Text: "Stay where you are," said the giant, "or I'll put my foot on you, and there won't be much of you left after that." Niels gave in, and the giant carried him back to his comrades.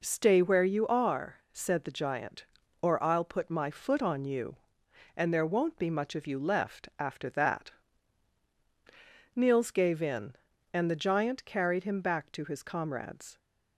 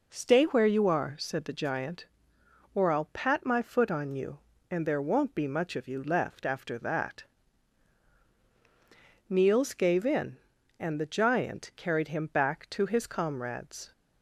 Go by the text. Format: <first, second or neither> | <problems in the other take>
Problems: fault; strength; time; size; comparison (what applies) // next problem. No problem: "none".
first | says "pat" for "put"; at 3.1 s